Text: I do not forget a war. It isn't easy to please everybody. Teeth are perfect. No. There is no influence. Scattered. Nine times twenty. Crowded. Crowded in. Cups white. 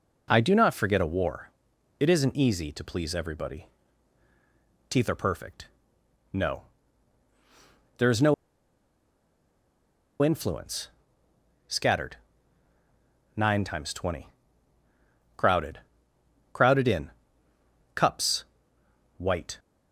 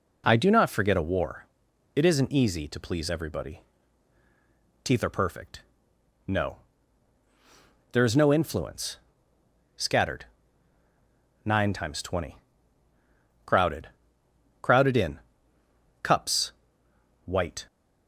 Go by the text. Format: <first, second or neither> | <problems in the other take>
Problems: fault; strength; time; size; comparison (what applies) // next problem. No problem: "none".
second | pauses between "no" and "influence"; strong; at 8.3 s; 1.8 s long // pauses between "Cups" and "white"; noticeable; at 18.4 s; 0.72 s long; noticeable in the second